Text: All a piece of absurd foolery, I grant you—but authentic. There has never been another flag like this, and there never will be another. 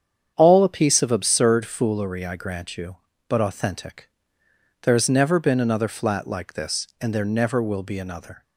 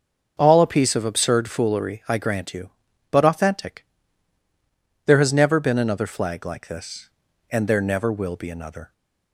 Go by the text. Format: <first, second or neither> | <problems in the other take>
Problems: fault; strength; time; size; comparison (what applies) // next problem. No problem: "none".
second | starts louder than the rest; strong; until 1.3 s; 8.5 dB; also in the second // says "flat" for "flag"; at 5.8 s